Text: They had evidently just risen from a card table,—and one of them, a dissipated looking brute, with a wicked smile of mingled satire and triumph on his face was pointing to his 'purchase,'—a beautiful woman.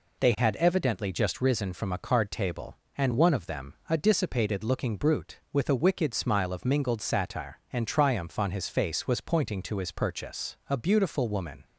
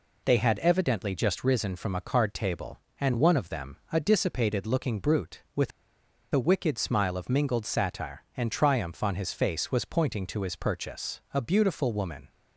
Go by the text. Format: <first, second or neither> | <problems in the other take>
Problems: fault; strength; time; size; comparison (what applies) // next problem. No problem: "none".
first | pauses between "with" and "a"; noticeable; at 5.7 s; 0.64 s long